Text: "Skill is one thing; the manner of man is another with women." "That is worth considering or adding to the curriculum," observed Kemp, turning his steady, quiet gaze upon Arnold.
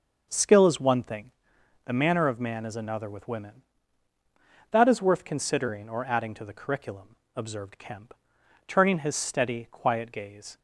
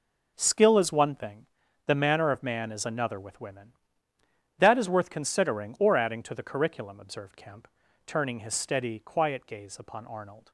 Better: second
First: starts louder than the rest; noticeable; until 1.3 s; 6 dB // stops before "upon Arnold"; at 10.5 s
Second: none

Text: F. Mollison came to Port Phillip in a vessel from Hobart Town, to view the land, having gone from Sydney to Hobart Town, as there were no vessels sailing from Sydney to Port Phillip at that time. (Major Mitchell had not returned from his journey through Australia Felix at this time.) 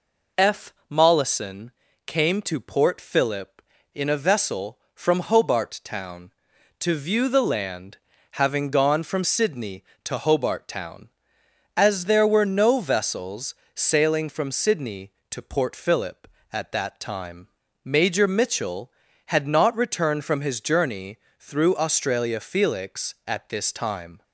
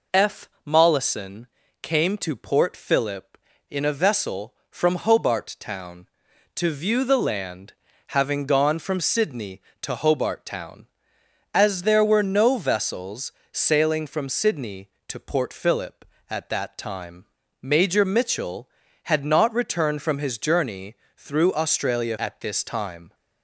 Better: first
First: pauses between "Mollison" and "came"; slight; at 1.7 s; 0.36 s long // pauses between "vessels" and "sailing"; slight; at 13.5 s; 0.22 s long // pauses between "journey" and "through"; slight; at 21.1 s; 0.20 s long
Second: pauses between "Mollison" and "came"; slight; at 1.4 s; 0.36 s long // pauses between "vessels" and "sailing"; slight; at 13.3 s; 0.22 s long // pauses between "journey" and "through"; slight; at 20.9 s; 0.20 s long // skips "Felix"; at 22.1 s

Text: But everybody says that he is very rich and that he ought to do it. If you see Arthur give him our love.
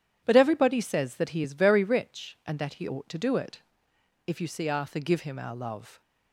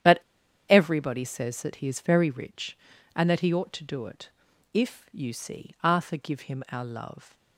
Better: first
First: starts louder than the rest; strong; until 1.2 s; 10 dB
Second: starts louder than the rest; strong; until 1.5 s; 10 dB // pauses between "But" and "everybody"; noticeable; at 0.2 s; 0.48 s long

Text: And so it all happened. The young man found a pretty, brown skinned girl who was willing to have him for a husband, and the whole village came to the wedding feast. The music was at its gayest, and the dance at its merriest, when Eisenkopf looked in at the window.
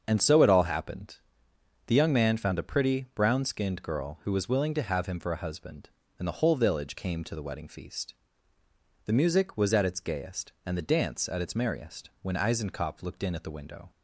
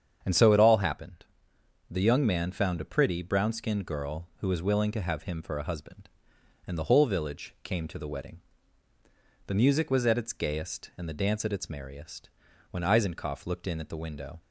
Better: first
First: starts louder than the rest; until 1.0 s; 7 dB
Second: starts louder than the rest; strong; until 1.2 s; 8 dB // skips "feast"; at 8.9 s

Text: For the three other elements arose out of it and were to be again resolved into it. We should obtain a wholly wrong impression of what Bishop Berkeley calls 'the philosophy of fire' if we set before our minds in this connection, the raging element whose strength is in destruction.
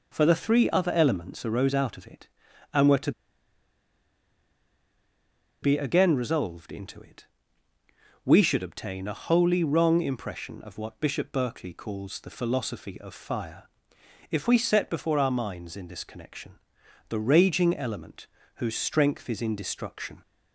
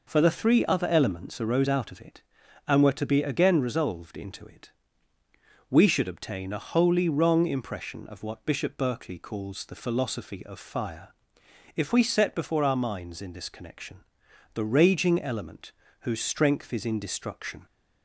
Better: second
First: pauses between "to" and "be"; strong; at 3.1 s; 2.5 s long // pauses between "fire" and "if"; noticeable; at 13.6 s; 0.62 s long // pauses between "element" and "whose"; slight; at 18.2 s; 0.30 s long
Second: pauses between "fire" and "if"; noticeable; at 11.1 s; 0.62 s long // pauses between "element" and "whose"; slight; at 15.7 s; 0.30 s long

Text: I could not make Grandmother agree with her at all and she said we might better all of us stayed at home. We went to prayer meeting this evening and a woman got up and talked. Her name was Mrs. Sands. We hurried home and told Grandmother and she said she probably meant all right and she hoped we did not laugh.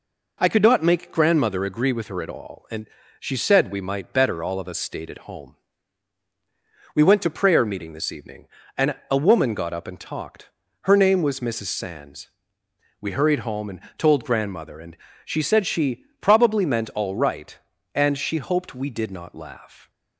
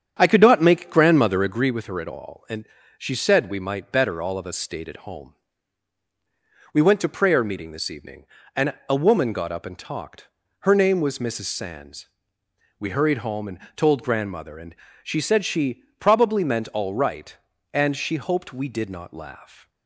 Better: first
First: pauses between "and" and "she"; slight; at 2.8 s; 0.32 s long // pauses between "and" and "a"; slight; at 8.9 s; 0.16 s long // pauses between "and" and "told"; slight; at 13.7 s; 0.18 s long // pauses between "and" and "she"; slight; at 14.9 s; 0.28 s long // pauses between "she" and "probably"; slight; at 16.0 s; 0.16 s long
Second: starts louder than the rest; strong; until 1.7 s; 8 dB // pauses between "and" and "she"; slight; at 2.6 s; 0.32 s long // pauses between "and" and "a"; slight; at 8.7 s; 0.16 s long // pauses between "and" and "told"; slight; at 13.5 s; 0.18 s long // pauses between "and" and "she"; slight; at 14.7 s; 0.28 s long // pauses between "she" and "probably"; slight; at 15.8 s; 0.16 s long

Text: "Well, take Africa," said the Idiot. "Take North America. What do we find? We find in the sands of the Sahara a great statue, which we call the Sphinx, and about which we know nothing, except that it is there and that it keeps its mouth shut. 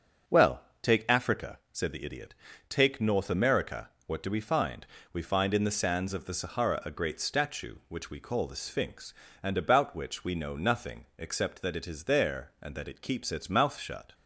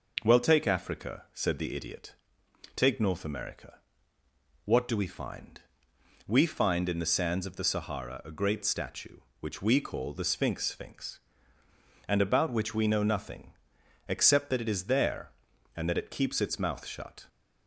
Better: first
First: none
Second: says "Sphinx" twice; at 10.6 s

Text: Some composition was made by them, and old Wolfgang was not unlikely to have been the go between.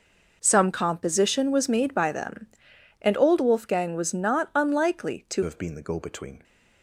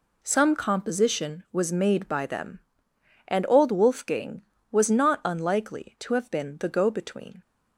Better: second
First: changes voice at "have"; from 5.4 s on; 1.0 s long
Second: none

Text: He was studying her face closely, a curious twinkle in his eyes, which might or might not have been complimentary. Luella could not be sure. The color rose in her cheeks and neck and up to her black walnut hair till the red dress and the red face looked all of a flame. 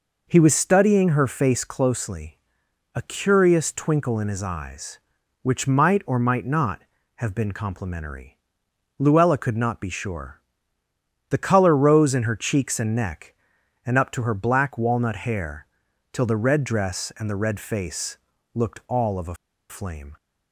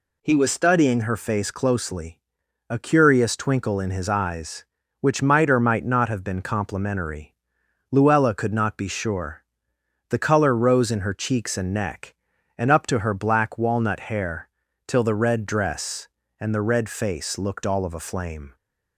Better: second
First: pauses between "hair" and "till"; noticeable; at 15.6 s; 0.46 s long // pauses between "face" and "looked"; slight; at 18.1 s; 0.36 s long // pauses between "a" and "flame"; slight; at 19.3 s; 0.34 s long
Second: pauses between "hair" and "till"; at 14.4 s; 0.38 s long

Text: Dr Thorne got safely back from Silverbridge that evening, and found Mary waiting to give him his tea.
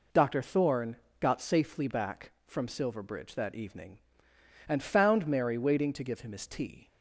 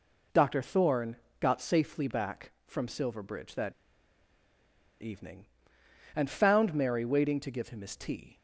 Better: first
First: pauses between "Thorne" and "got"; slight; at 0.9 s; 0.24 s long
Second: pauses between "Thorne" and "got"; slight; at 1.1 s; 0.24 s long // pauses between "that" and "evening"; strong; at 3.7 s; 1.2 s long

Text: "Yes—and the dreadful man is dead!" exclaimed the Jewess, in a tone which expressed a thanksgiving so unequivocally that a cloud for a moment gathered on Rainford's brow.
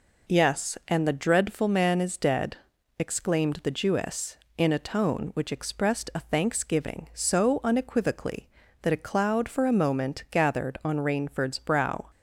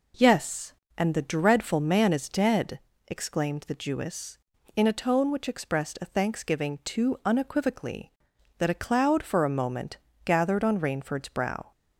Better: first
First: none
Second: says "too" for "so"; at 6.8 s // pauses between "moment" and "gathered"; slight; at 9.9 s; 0.26 s long

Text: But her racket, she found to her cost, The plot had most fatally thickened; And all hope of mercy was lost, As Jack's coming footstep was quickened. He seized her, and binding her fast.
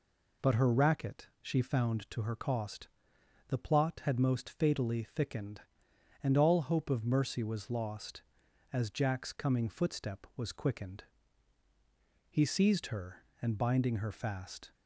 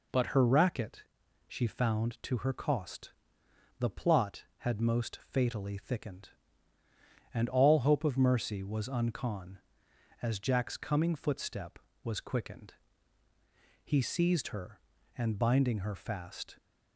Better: first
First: none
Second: says "uncon" for "lost"; at 8.8 s

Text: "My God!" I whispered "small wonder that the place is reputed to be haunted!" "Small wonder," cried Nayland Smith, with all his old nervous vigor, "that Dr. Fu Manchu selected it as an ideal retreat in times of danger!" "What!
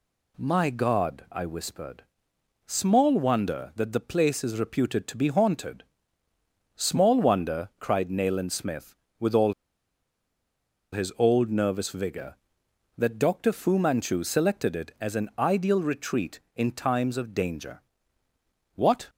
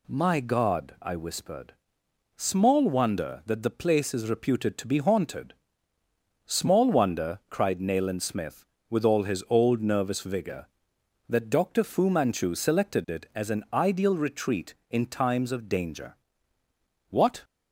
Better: second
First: pauses between "whispered" and "small"; noticeable; at 2.0 s; 0.64 s long // pauses between "all" and "his"; strong; at 9.5 s; 1.3 s long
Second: pauses between "whispered" and "small"; noticeable; at 1.7 s; 0.64 s long

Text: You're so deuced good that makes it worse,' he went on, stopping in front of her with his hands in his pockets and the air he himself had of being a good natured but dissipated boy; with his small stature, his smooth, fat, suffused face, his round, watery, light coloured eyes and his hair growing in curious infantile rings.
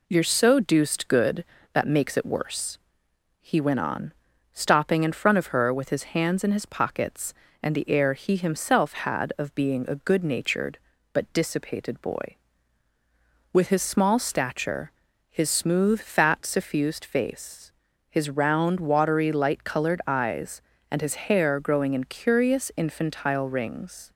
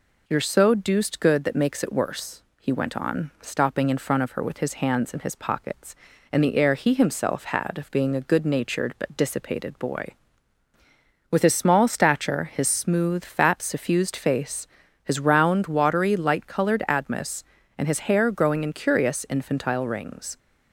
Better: first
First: none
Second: says "admis" for "eyes"; at 16.8 s

